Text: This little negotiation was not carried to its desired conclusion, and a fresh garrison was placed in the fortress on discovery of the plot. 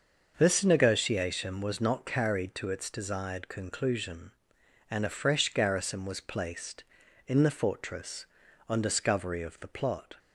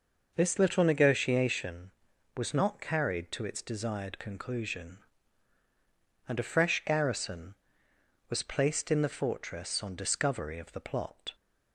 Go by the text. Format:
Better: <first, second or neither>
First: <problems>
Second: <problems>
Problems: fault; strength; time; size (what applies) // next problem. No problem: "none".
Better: second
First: starts louder than the rest; until 1.3 s; 6.5 dB // skips "little"; at 0.6 s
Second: none